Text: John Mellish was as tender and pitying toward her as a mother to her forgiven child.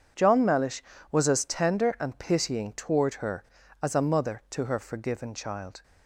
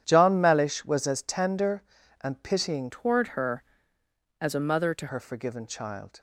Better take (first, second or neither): first